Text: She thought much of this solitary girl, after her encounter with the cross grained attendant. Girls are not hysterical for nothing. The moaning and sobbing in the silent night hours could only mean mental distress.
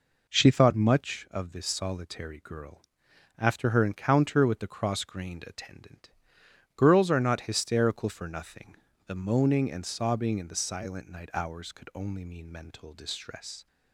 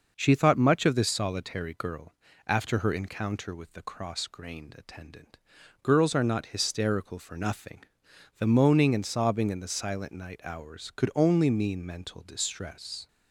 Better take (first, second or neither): neither